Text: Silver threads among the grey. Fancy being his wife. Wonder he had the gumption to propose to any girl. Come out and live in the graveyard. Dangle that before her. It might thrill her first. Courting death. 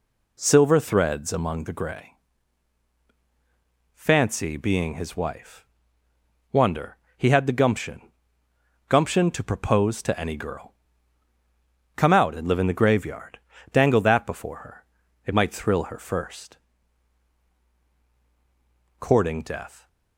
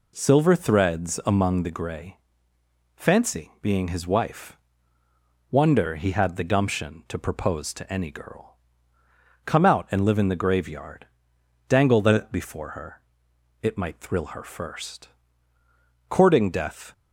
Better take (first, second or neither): second